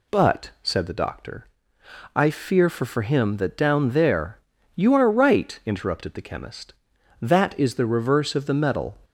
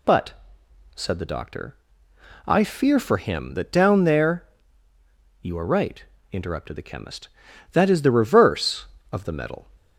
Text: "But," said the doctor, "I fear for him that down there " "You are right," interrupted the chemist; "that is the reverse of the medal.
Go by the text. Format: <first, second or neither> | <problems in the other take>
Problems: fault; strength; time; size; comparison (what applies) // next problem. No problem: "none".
second | says "for" twice; at 2.8 s